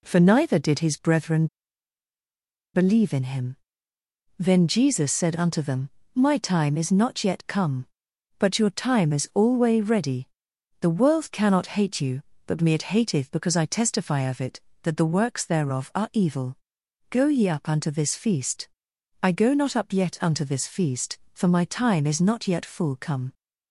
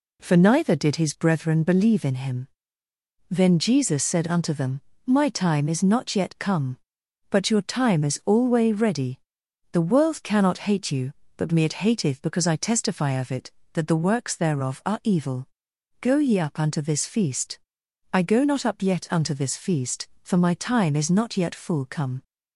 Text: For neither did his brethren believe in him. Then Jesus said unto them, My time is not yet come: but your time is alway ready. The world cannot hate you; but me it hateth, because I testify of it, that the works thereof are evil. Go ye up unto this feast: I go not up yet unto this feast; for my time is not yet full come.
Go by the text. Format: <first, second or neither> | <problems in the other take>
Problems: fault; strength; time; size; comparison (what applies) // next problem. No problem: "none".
second | pauses between "brethren" and "believe"; strong; at 1.4 s; 1.2 s long